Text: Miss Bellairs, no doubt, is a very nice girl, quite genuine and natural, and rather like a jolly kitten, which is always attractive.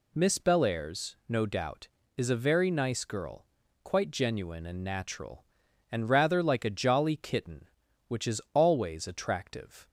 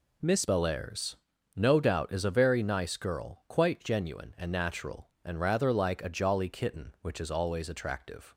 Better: first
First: none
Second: changes voice at "Bellairs"; from 0.4 s on; 7.9 s long

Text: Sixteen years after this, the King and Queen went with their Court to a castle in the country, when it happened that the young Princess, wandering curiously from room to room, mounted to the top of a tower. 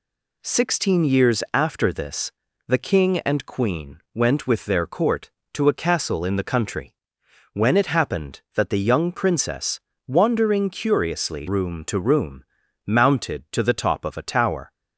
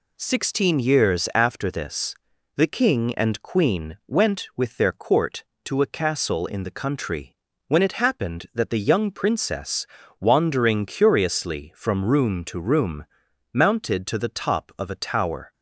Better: second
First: pauses between "Queen" and "went"; slight; at 3.9 s; 0.16 s long // skips "from"; at 11.4 s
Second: none

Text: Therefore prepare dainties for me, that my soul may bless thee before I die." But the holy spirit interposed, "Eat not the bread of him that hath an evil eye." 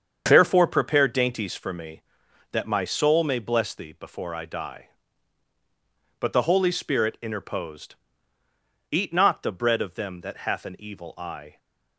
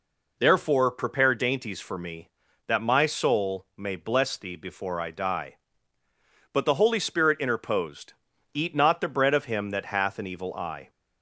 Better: second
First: starts louder than the rest; strong; until 1.2 s; 7.5 dB // says "them" for "him"; at 9.9 s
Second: none

